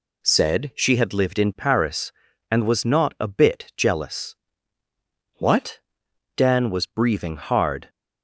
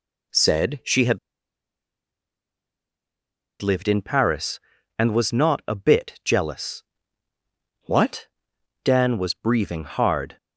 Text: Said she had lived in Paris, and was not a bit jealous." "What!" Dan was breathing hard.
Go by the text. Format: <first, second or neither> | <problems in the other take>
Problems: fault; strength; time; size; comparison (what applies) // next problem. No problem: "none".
first | pauses between "had" and "lived"; strong; at 1.1 s; 2.4 s long